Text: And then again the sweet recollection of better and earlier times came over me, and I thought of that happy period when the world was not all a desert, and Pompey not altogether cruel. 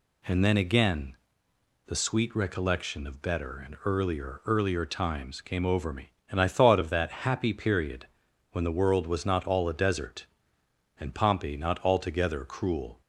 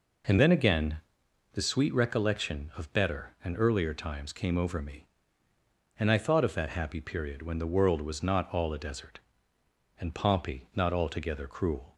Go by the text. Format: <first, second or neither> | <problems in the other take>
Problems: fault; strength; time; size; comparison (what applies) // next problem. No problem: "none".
second | pauses between "again" and "the"; noticeable; at 1.1 s; 0.70 s long; noticeable in the second // says "earlier" twice; at 4.4 s // pauses between "period" and "when"; noticeable; at 8.0 s; 0.46 s long